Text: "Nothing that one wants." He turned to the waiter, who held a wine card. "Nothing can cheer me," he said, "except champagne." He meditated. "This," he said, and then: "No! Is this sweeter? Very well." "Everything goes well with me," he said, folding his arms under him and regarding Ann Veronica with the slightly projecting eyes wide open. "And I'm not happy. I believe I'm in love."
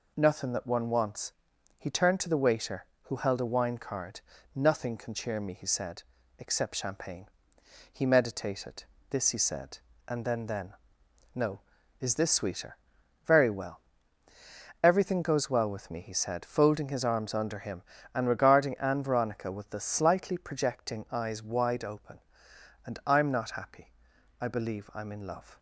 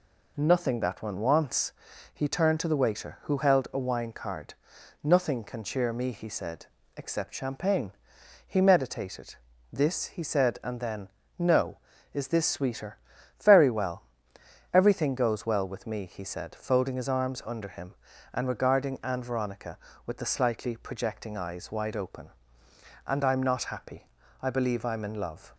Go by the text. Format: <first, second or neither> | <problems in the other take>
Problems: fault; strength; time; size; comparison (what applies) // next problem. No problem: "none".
second | says "then" twice; at 10.4 s